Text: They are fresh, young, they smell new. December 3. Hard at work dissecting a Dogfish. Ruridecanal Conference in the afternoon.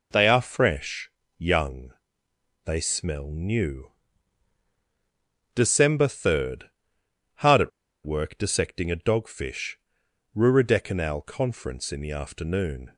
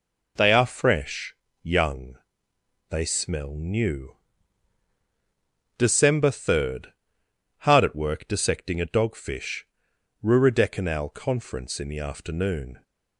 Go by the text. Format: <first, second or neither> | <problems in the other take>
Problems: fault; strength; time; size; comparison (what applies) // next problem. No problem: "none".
second | pauses between "at" and "work"; slight; at 7.7 s; 0.34 s long